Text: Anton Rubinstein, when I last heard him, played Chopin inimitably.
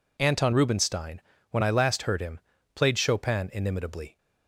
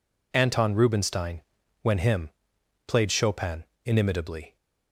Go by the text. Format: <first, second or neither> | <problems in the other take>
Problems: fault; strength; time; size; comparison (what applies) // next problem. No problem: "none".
first | skips "I last heard"; at 1.9 s // pauses between "Chopin" and "inimitably"; slight; at 3.6 s; 0.20 s long